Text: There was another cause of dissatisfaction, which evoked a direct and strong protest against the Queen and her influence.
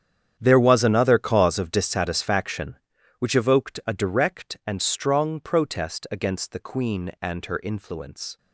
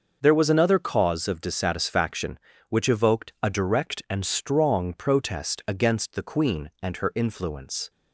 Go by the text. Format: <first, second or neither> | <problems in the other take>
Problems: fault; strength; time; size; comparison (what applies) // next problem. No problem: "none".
second | gets quieter; strong; throughout; 14 dB // starts louder than the rest; strong; until 1.3 s; 8.5 dB; also in the second